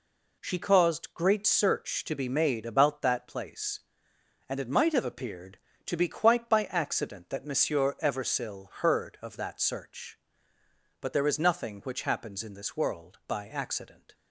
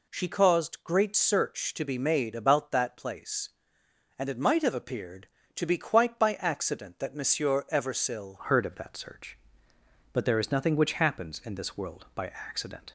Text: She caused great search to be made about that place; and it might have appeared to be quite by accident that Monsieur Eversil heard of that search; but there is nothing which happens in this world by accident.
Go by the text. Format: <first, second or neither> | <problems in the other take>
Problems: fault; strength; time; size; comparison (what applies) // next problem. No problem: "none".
first | changes voice at "heard"; from 8.4 s on; 4.5 s long